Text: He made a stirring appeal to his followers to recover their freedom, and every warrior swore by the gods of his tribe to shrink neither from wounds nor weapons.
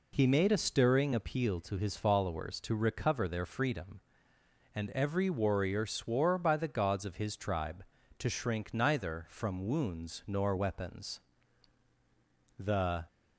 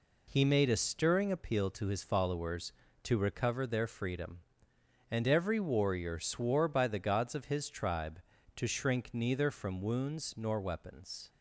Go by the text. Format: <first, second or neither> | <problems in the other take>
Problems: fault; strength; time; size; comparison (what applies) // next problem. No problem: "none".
second | goes on to say "The"; slight; from 12.5 s on; 0.48 s long